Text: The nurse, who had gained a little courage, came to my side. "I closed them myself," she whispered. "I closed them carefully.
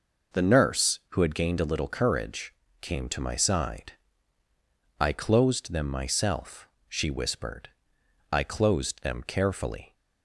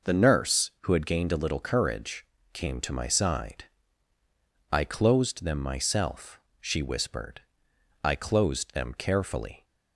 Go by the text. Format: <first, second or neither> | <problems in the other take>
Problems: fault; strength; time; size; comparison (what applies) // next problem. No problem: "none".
neither | none